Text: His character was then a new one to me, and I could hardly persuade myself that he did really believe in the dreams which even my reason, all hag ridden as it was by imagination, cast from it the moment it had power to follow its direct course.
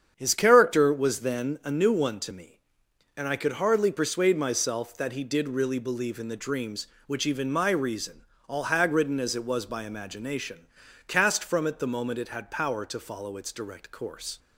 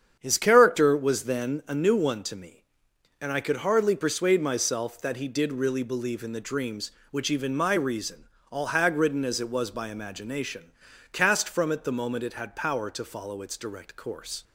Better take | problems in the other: neither | starts louder than the rest; strong; the same in both

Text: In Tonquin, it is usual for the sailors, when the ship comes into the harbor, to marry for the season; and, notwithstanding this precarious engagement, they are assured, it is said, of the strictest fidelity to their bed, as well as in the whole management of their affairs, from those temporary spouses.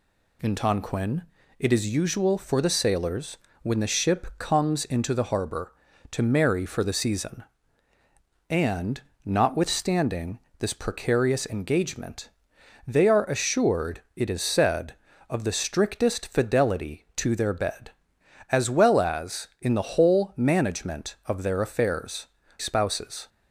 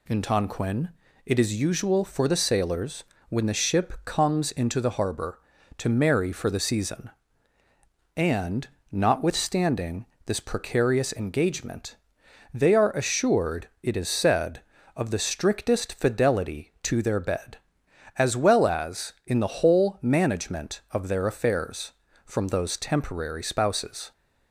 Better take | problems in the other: second | pauses between "notwithstanding" and "this"; slight; at 10.3 s; 0.20 s long; slight in the second // skips "from those temporary"; at 22.4 s

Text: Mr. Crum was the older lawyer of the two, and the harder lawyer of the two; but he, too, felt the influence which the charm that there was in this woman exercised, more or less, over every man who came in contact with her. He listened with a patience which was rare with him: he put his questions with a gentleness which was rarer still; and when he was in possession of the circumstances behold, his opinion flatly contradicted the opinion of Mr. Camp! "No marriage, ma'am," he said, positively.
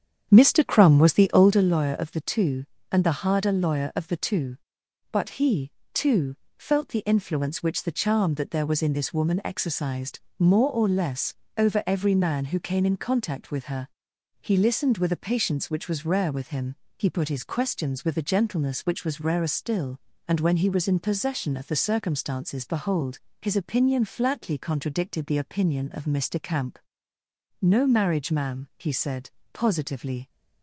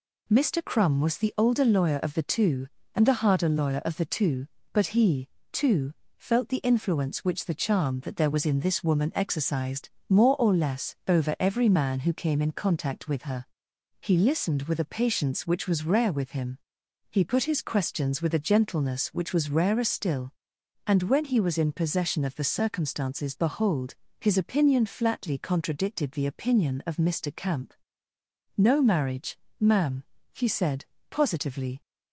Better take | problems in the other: second | starts louder than the rest; strong; until 1.7 s; 8.5 dB

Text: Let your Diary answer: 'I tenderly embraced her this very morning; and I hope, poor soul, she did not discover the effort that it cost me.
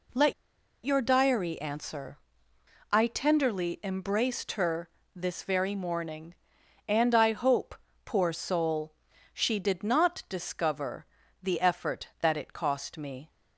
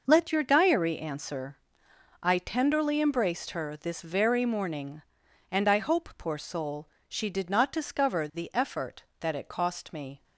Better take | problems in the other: second | pauses between "Let" and "your"; noticeable; at 0.3 s; 0.51 s long // pauses between "her" and "this"; slight; at 4.9 s; 0.24 s long // pauses between "discover" and "the"; slight; at 11.0 s; 0.34 s long

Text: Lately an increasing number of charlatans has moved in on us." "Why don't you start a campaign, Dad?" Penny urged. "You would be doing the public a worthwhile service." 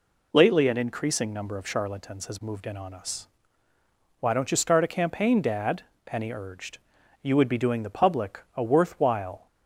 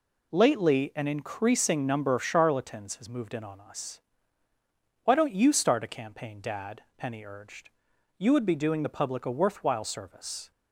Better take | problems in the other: second | stops before "service"; at 9.4 s

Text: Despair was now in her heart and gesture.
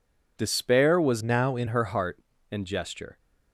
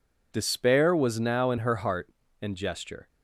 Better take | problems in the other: second | changes voice from "now" to "in"; from 1.2 to 1.6 s; 0.4 s long

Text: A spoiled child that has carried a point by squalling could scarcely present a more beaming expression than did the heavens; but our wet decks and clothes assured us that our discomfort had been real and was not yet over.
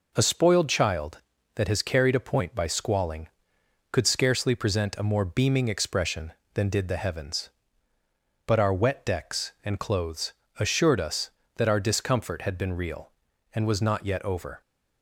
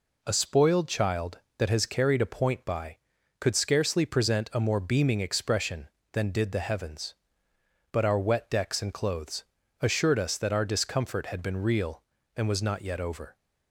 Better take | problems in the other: first | skips "squalling"; at 3.1 s // pauses between "clothes" and "assured"; slight; at 9.4 s; 0.36 s long; slight in the first

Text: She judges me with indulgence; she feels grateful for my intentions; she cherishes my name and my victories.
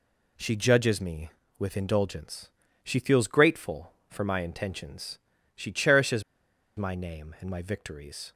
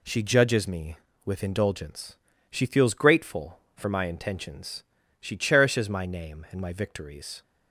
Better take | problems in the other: second | pauses between "cherishes" and "my"; noticeable; at 6.2 s; 0.56 s long

